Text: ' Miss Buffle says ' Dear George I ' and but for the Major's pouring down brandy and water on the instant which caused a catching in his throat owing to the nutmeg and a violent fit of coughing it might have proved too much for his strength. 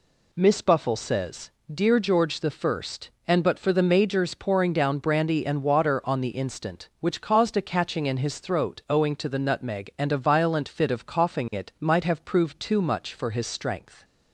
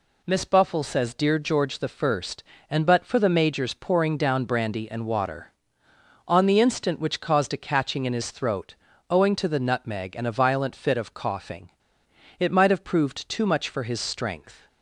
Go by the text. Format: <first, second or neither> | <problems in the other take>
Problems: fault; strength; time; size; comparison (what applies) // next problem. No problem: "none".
first | pauses between "throat" and "owing"; slight; at 8.7 s; 0.34 s long // pauses between "coughing" and "it"; noticeable; at 11.7 s; 0.68 s long